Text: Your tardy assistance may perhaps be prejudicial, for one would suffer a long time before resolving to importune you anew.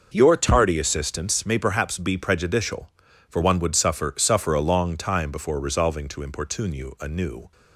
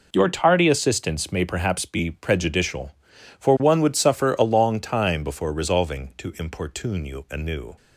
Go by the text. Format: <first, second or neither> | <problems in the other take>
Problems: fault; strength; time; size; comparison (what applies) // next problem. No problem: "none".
second | says "suffer" twice; at 4.1 s